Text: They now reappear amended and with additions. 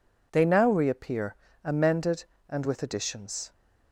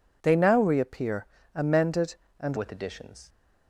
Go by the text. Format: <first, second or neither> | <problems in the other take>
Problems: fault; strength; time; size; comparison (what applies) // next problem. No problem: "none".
first | pauses between "reappear" and "amended"; slight; at 1.2 s; 0.28 s long; slight in the first // changes voice at "with"; from 2.5 s on; 0.7 s long